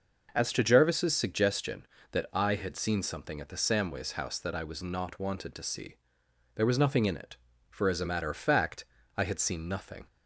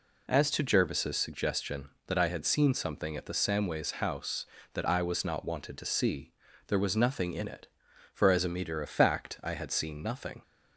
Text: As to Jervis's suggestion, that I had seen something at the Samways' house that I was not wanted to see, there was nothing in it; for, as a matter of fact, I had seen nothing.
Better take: first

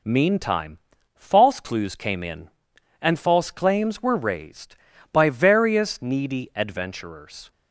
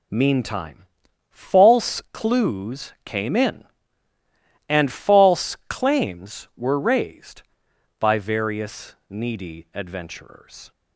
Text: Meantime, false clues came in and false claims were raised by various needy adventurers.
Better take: neither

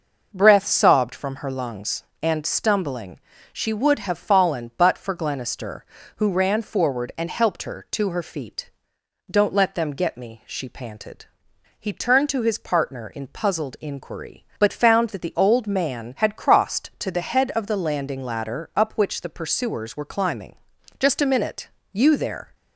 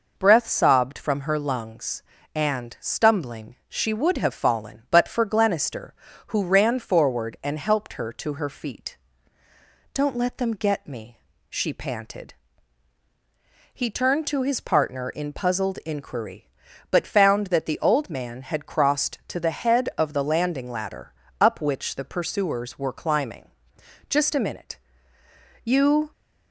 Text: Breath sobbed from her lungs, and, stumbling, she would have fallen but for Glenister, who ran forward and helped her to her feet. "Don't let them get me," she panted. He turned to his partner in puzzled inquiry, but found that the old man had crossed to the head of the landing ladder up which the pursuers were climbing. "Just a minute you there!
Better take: first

